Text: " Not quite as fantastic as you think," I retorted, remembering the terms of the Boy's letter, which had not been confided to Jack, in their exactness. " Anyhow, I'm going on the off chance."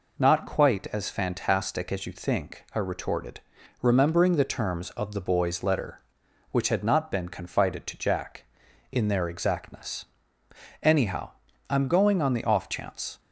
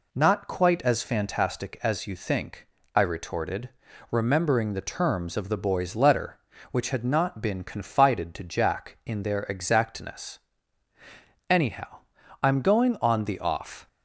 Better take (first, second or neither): first